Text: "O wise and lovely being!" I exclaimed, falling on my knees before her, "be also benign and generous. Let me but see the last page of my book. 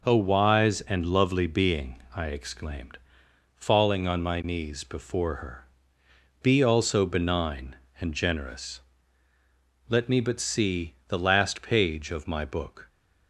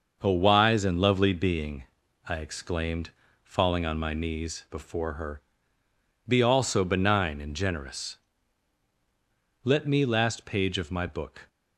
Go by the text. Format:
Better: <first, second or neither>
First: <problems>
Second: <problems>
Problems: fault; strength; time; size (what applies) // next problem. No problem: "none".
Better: first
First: none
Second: starts louder than the rest; noticeable; until 1.2 s; 6 dB // skips "but see the"; at 10.0 s